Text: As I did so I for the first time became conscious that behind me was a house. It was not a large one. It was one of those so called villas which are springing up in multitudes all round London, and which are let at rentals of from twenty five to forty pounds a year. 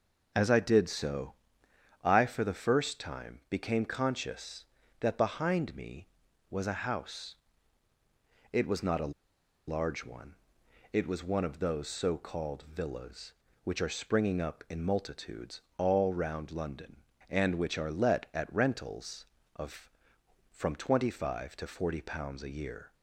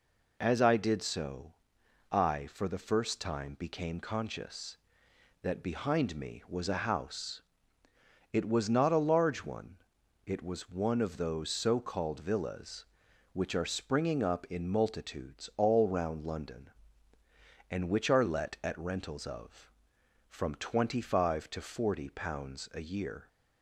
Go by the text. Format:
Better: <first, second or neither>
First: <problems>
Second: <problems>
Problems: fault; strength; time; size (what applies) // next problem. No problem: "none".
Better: second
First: pauses between "so" and "I"; noticeable; at 1.3 s; 0.68 s long // pauses between "a" and "large"; noticeable; at 9.1 s; 0.54 s long // pauses between "multitudes" and "all"; slight; at 15.5 s; 0.18 s long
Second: pauses between "so" and "I"; noticeable; at 1.5 s; 0.58 s long